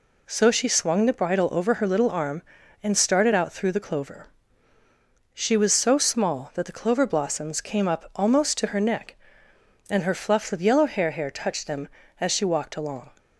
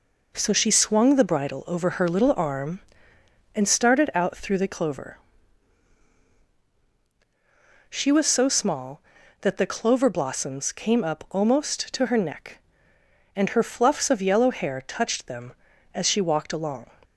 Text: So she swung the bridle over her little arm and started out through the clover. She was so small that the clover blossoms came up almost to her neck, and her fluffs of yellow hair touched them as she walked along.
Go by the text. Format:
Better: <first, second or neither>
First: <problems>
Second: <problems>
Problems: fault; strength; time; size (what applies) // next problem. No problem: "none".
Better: second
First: says "hair" twice; at 11.0 s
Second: none